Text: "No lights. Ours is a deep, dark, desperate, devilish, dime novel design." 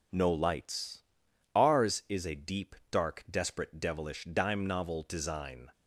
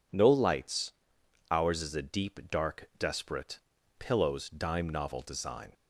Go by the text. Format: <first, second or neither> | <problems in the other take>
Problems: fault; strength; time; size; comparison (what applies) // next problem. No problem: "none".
first | says "pillows" for "devilish"; at 3.9 s